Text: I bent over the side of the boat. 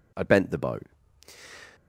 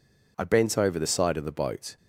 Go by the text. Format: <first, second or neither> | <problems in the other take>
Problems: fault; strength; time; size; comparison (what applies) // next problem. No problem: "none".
second | skips "over the side of"; at 0.4 s